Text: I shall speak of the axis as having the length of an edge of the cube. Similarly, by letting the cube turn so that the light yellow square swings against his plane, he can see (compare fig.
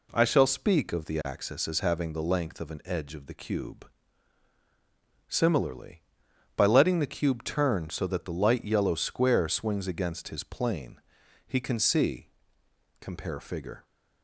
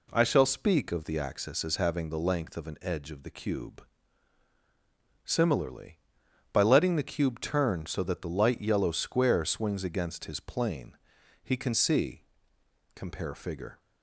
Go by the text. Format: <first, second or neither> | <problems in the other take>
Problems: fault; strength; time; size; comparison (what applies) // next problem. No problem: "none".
neither | none